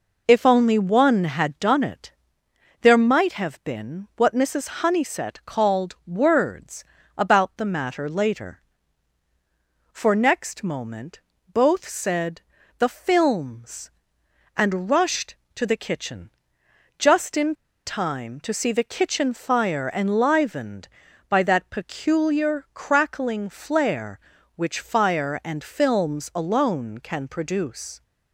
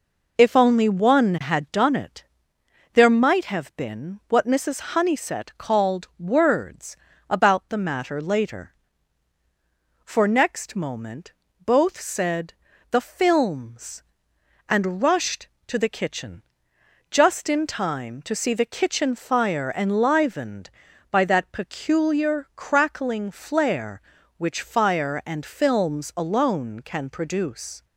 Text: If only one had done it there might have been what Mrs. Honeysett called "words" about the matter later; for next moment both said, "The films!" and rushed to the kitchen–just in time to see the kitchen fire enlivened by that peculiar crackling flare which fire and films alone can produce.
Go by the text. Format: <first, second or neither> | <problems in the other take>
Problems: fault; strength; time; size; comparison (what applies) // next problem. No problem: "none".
second | pauses between "it" and "there"; noticeable; at 2.1 s; 0.70 s long; noticeable in the second // pauses between "words" and "about"; slight; at 6.8 s; 0.32 s long; slight in the second // pauses between "moment" and "both"; slight; at 11.1 s; 0.32 s long; slight in the second // pauses between "in" and "time"; slight; at 17.5 s; 0.30 s long